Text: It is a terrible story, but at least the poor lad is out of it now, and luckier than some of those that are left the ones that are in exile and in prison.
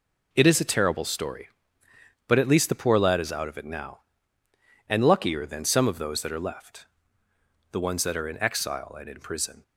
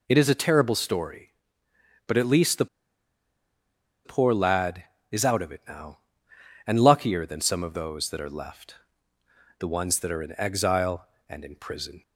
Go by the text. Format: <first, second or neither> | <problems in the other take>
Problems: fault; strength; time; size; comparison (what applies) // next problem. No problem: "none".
first | pauses between "the" and "poor"; strong; at 2.6 s; 1.3 s long // pauses between "left" and "the"; noticeable; at 8.7 s; 0.82 s long; noticeable in the first